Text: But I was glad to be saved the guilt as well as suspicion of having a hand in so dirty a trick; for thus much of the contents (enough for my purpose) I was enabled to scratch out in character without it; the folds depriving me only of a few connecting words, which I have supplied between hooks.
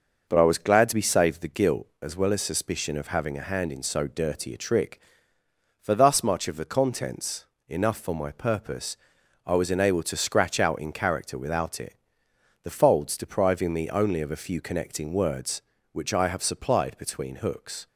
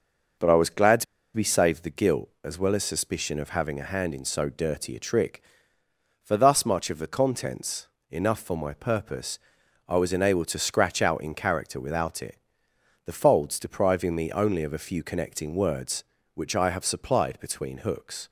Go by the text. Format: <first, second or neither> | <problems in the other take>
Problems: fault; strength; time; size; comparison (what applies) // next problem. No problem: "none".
first | pauses between "to" and "be"; slight; at 1.0 s; 0.31 s long